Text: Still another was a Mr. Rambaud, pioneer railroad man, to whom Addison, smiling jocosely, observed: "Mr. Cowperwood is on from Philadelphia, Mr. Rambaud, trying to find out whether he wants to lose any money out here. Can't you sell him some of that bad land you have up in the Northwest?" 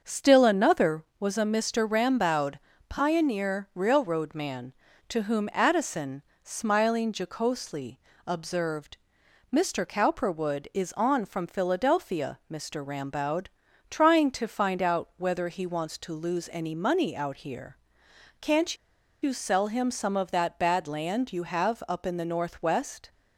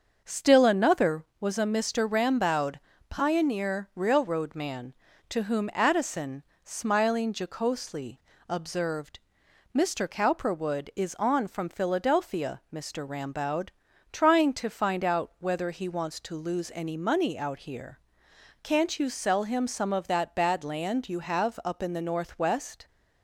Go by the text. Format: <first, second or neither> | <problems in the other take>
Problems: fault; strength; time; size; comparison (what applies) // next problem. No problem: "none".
second | starts louder than the rest; until 1.0 s; 7 dB; also in the second // pauses between "Can't" and "you"; at 18.7 s; 0.45 s long